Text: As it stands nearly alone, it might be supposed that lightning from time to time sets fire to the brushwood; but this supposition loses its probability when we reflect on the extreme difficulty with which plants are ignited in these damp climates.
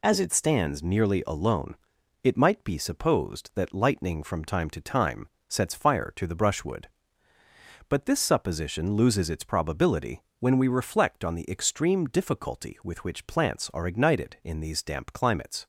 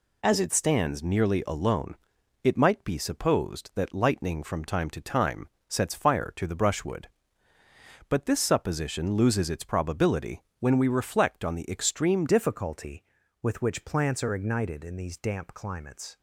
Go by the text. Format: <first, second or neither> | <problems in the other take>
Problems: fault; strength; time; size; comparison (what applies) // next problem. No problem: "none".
first | pauses between "time" and "sets"; slight; at 5.4 s; 0.20 s long; slight in the first // pauses between "probability" and "when"; slight; at 10.4 s; 0.16 s long; slight in the first // changes voice at "difficulty"; from 12.2 s on; 3.9 s long